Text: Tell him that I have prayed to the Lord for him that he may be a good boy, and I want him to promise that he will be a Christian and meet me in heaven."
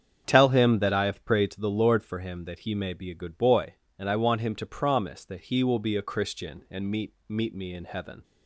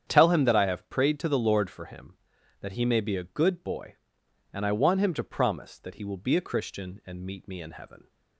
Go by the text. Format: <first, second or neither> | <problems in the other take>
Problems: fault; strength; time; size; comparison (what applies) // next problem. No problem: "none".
second | starts louder than the rest; strong; until 1.2 s; 7.5 dB; strong in the second // says "meet" twice; at 7.2 s